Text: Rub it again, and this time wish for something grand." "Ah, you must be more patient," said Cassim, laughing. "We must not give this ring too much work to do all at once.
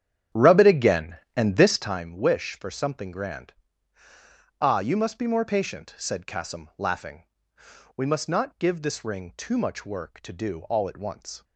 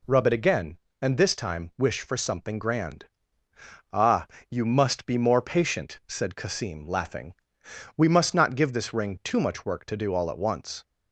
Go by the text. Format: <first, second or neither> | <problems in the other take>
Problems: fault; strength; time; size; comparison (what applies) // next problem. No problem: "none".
second | starts louder than the rest; strong; until 2.0 s; 9 dB